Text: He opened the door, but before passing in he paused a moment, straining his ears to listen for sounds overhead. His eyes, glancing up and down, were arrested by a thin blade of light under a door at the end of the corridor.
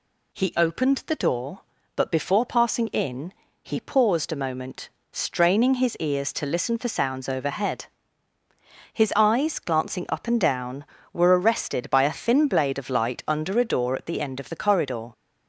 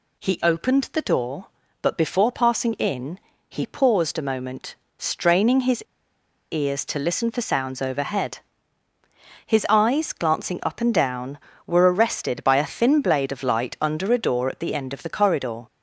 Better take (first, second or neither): first